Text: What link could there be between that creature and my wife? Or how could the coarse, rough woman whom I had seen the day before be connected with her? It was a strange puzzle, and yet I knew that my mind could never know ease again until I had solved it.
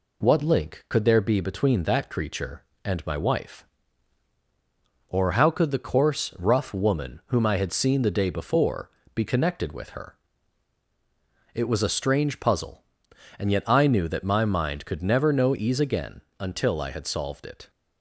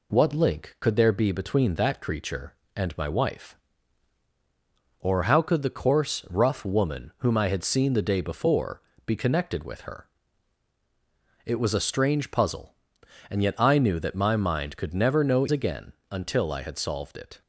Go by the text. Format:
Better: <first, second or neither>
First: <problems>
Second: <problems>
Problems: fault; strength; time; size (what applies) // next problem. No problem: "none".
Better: first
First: pauses between "before" and "be"; slight; at 8.8 s; 0.24 s long // pauses between "again" and "until"; slight; at 16.1 s; 0.18 s long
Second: pauses between "before" and "be"; slight; at 8.8 s; 0.24 s long // skips "ease"; at 15.4 s // pauses between "again" and "until"; slight; at 15.9 s; 0.18 s long